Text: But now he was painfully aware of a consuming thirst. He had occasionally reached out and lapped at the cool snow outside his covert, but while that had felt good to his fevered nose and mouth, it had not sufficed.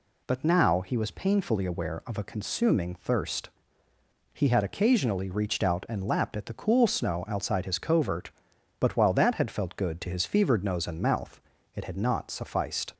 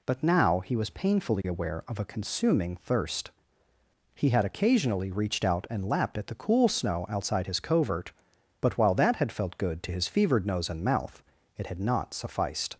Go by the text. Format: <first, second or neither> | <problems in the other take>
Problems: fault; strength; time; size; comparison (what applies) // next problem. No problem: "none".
neither | none